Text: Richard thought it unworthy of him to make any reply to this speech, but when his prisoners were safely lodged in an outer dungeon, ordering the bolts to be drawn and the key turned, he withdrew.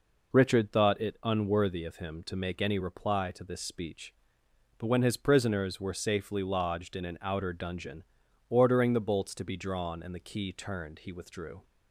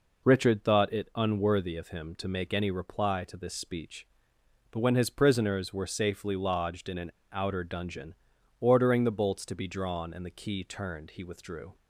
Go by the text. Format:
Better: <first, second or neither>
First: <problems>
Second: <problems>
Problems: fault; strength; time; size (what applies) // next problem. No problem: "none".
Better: first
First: none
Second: pauses between "an" and "outer"; slight; at 7.1 s; 0.19 s long